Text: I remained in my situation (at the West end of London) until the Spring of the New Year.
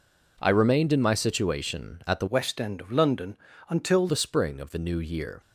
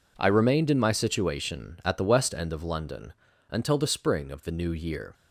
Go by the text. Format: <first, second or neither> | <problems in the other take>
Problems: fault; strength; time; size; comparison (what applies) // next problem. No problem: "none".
second | changes voice from "West" to "until"; from 2.2 to 4.0 s; 1.8 s long